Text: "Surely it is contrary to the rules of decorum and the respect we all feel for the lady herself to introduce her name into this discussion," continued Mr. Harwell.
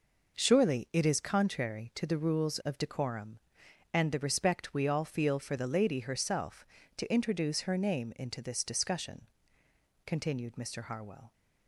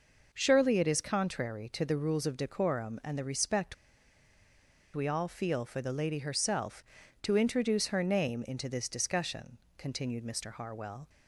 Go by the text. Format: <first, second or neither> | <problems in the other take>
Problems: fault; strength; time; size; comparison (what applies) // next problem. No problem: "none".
first | pauses between "respect" and "we"; at 3.7 s; 1.2 s long